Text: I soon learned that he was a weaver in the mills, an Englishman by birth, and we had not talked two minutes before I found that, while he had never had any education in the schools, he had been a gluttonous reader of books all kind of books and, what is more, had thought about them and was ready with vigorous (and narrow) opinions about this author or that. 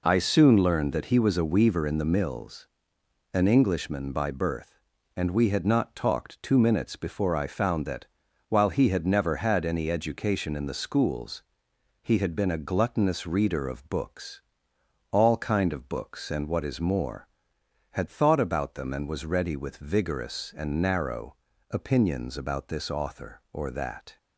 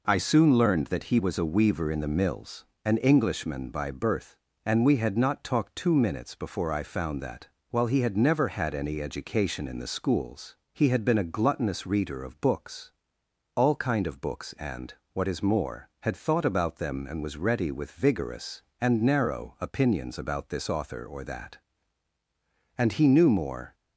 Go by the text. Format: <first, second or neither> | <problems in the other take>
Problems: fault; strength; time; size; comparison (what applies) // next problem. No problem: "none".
first | pauses between "books" and "all"; noticeable; at 12.9 s; 0.66 s long; noticeable in the first // goes on to say "And he knew more"; noticeable; from 22.7 s on; 0.98 s long